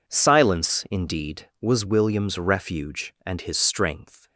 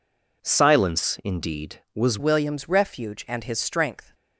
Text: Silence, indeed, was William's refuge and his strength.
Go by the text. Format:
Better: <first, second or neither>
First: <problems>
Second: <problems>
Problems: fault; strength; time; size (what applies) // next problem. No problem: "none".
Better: first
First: none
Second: changes voice at "William's"; from 2.1 s on; 2.0 s long